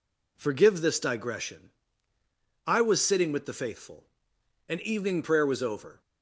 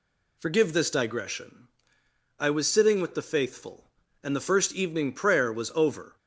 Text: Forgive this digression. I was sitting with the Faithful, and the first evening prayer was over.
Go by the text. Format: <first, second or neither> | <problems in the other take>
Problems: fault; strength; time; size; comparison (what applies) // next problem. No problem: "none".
second | skips "the first"; at 4.8 s